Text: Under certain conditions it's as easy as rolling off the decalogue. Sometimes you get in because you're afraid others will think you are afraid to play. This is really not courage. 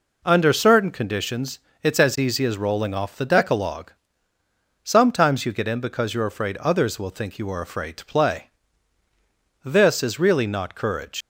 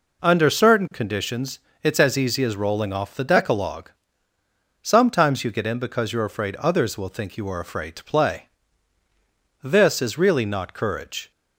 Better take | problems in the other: second | pauses between "conditions" and "it's"; slight; at 1.5 s; 0.24 s long; slight in the second // leaves "courage" unfinished; at 11.2 s; 115 ms

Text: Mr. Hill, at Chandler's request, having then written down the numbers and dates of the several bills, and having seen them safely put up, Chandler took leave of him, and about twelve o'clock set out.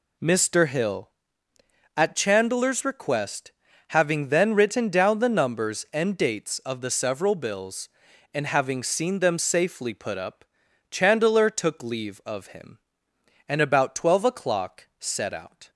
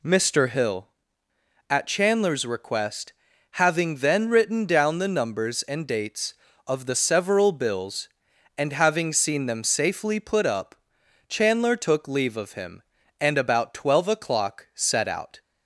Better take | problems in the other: neither | none

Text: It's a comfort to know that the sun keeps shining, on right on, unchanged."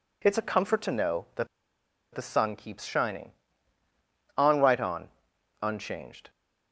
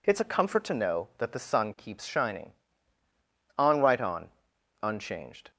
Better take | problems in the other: second | pauses between "that" and "the"; noticeable; at 1.4 s; 0.66 s long

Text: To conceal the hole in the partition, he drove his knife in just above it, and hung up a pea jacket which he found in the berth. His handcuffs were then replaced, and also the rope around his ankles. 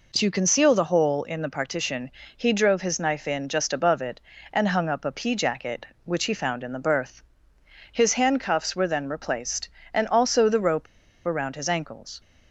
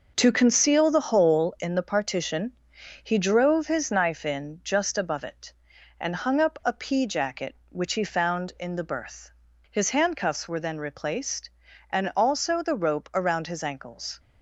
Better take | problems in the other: second | pauses between "rope" and "around"; at 10.8 s; 0.41 s long

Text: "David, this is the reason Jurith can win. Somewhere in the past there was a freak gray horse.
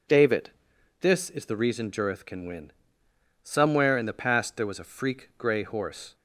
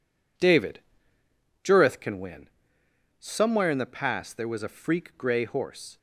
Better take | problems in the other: first | skips "this is the reason"; at 1.2 s

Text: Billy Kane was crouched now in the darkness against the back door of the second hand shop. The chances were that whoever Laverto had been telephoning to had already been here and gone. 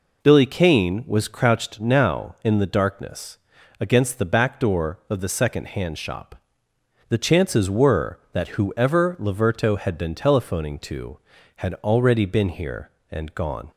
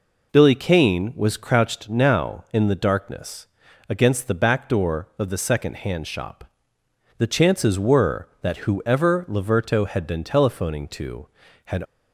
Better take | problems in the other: first | pauses between "darkness" and "against"; at 3.4 s; 0.40 s long; also in the first // stops before "already been here and gone"; at 11.8 s

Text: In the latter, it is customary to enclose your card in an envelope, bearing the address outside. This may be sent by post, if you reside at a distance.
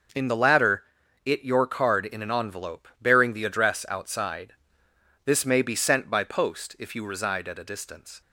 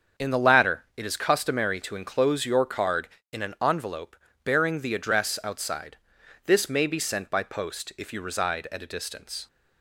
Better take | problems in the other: second | starts louder than the rest; until 1.5 s; 6.5 dB; also in the second // skips "is customary to enclose"; at 1.4 s

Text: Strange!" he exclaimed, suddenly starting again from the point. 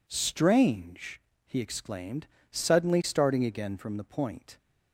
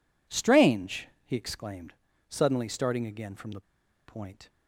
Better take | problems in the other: first | pauses between "the" and "point"; noticeable; at 3.6 s; 0.46 s long

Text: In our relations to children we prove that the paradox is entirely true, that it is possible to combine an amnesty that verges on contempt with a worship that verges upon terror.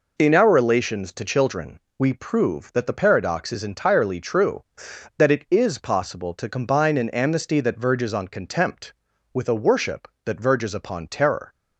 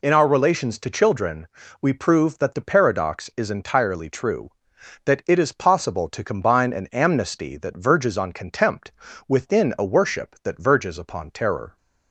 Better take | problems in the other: first | pauses between "children" and "we"; slight; at 1.4 s; 0.36 s long; slight in the first // says "within" for "with"; at 9.2 s

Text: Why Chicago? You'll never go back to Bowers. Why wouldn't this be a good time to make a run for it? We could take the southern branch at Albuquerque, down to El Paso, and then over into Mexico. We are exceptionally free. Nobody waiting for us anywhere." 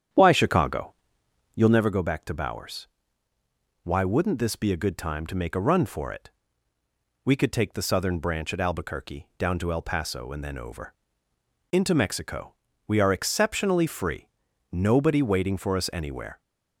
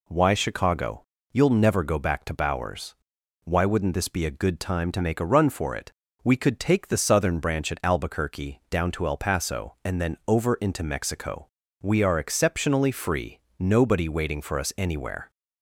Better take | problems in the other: second | starts louder than the rest; strong; until 1.9 s; 9 dB // pauses between "over" and "into"; noticeable; at 10.9 s; 0.78 s long

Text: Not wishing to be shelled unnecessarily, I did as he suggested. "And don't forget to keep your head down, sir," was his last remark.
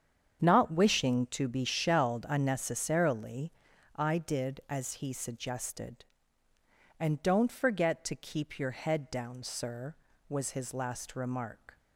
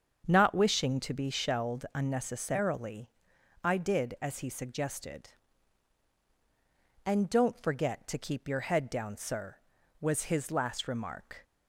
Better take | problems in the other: neither | starts louder than the rest; the same in both

